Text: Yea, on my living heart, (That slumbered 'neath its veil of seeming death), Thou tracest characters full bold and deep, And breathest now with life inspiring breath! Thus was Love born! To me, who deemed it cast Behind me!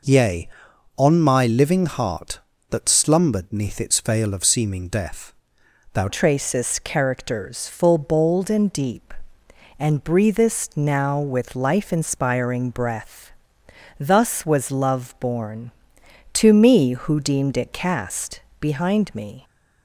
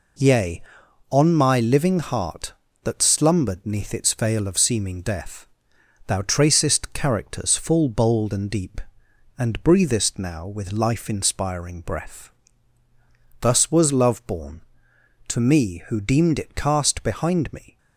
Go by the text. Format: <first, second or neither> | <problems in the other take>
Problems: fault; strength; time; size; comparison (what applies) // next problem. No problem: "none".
second | changes voice at "tracest"; from 6.0 s on; 13.4 s long // pauses between "cast" and "Behind"; slight; at 18.3 s; 0.18 s long